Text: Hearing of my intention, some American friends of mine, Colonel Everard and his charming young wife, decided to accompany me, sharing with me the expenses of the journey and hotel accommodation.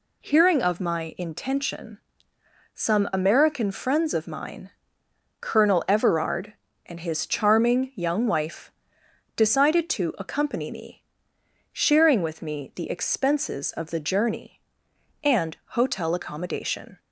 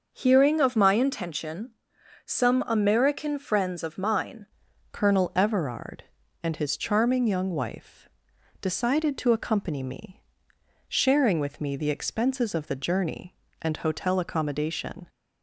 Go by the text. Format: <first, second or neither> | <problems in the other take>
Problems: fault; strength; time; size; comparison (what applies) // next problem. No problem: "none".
first | starts louder than the rest; until 1.1 s; 6 dB // changes voice at "Colonel"; from 4.9 s on; 10.1 s long